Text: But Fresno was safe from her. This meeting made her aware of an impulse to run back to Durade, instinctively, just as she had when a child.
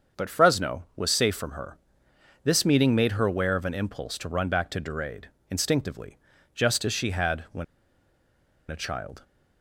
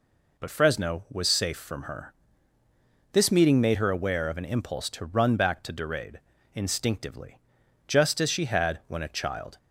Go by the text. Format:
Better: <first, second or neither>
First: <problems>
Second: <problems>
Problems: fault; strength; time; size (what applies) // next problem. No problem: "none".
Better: second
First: starts louder than the rest; until 1.2 s; 7 dB // pauses between "when" and "a"; at 7.6 s; 1.0 s long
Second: none